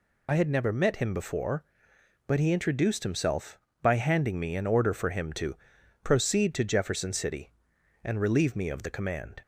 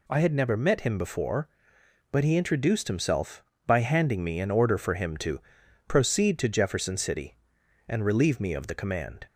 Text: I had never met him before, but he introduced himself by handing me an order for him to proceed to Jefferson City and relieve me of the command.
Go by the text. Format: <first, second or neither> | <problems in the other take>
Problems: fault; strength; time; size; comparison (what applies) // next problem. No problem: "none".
second | loses the start of "I"; at 0.2 s; 50 ms // pauses between "to" and "proceed"; noticeable; at 5.5 s; 0.48 s long; noticeable in the second